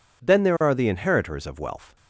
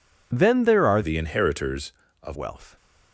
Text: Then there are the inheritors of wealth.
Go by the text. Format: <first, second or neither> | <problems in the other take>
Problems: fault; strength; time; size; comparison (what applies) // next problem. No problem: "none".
first | changes voice from "the" to "of"; from 1.0 to 2.3 s; 1.3 s long